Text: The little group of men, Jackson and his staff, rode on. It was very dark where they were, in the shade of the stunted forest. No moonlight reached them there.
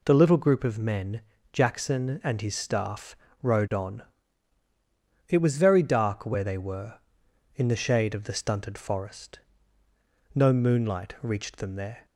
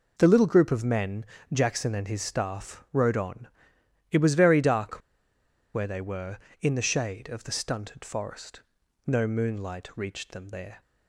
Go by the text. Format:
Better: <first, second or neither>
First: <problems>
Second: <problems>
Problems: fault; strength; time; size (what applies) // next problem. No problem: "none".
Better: first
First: none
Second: pauses between "dark" and "where"; noticeable; at 4.9 s; 0.75 s long